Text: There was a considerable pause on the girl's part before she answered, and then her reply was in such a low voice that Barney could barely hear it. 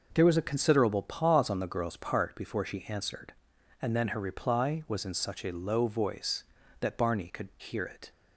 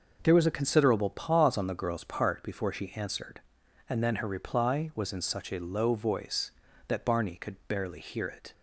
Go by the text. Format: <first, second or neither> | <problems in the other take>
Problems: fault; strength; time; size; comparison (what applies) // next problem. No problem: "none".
second | skips "barely"; at 7.5 s